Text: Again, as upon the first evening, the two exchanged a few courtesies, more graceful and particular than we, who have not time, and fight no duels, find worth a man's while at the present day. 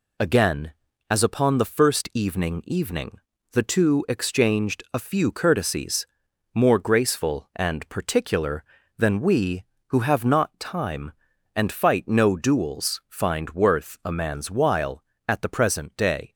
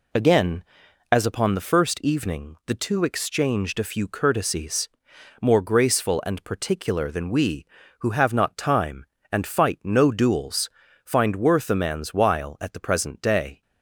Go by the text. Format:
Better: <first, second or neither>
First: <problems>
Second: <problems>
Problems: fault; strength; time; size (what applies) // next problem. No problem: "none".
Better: second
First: says "evening" twice; at 2.6 s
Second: none